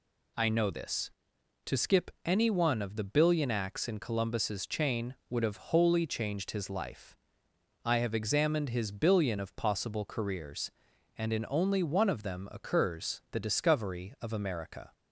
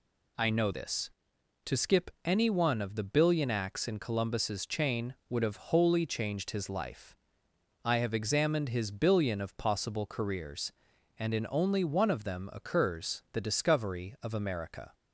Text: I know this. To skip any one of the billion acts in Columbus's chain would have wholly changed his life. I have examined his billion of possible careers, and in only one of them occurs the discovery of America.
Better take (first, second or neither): neither